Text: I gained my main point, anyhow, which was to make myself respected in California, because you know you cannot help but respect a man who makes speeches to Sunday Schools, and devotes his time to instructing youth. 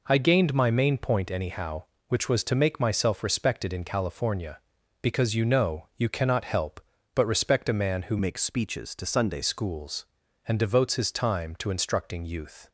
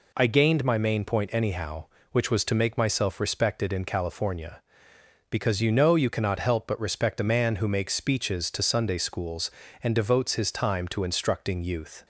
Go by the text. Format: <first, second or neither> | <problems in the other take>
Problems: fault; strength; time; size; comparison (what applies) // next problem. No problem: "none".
second | changes voice from "makes" to "Sunday"; from 8.1 to 9.4 s; 1.3 s long